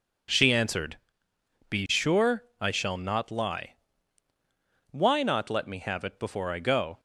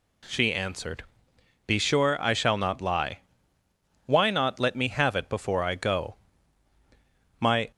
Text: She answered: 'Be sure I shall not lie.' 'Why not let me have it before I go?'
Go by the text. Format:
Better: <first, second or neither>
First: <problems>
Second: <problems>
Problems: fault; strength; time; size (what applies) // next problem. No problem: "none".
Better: first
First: none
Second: goes on to say "My"; slight; from 7.3 s on; 0.32 s long